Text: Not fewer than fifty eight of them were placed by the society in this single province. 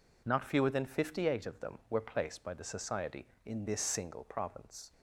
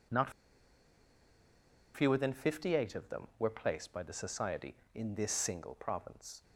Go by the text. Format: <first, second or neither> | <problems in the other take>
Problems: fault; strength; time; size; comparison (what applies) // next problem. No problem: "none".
first | pauses between "Not" and "fewer"; strong; at 0.3 s; 1.6 s long